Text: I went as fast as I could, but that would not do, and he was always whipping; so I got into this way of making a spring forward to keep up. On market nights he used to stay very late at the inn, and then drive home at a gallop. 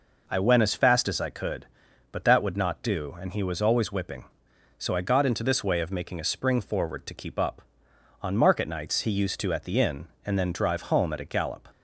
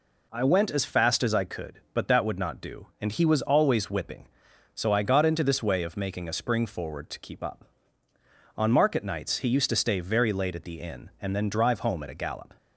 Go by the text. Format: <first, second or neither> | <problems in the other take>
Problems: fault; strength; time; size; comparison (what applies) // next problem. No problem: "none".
second | skips "stay very late"; at 9.5 s